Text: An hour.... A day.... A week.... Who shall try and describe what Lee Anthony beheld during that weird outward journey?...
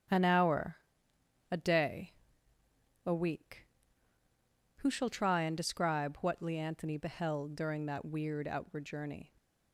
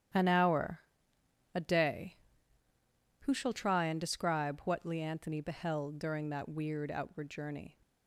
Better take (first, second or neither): first